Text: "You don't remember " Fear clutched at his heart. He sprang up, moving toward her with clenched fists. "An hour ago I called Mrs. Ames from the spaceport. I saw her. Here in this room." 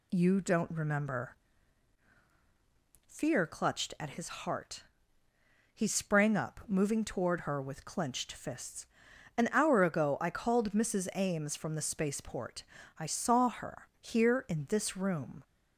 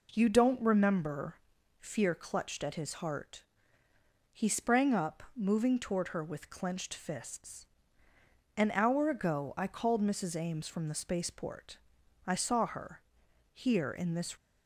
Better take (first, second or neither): first